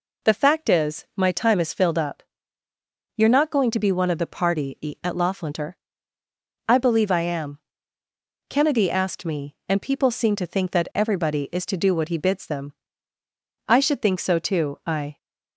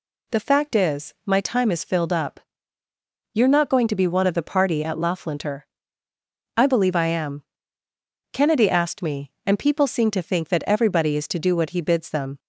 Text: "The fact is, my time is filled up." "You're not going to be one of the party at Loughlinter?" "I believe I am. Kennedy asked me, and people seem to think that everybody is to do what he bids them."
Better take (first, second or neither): second